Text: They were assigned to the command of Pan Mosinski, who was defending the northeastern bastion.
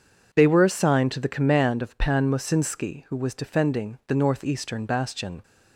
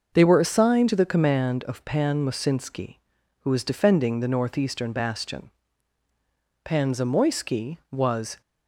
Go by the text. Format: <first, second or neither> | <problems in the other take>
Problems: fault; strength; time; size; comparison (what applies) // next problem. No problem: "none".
first | goes on to say "Pan Zamoyski was"; strong; from 6.6 s on; 1.7 s long